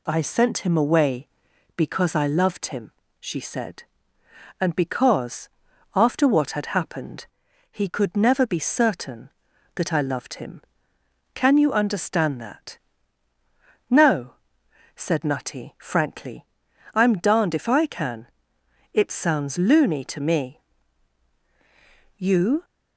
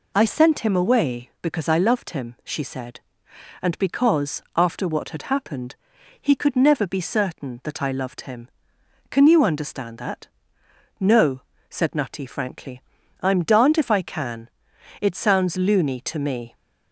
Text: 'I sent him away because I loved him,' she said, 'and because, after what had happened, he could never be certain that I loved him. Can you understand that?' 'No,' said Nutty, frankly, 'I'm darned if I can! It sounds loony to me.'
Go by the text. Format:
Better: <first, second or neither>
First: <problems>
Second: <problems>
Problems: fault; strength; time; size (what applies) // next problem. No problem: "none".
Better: second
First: goes on to say "You"; slight; from 22.1 s on; 0.48 s long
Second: none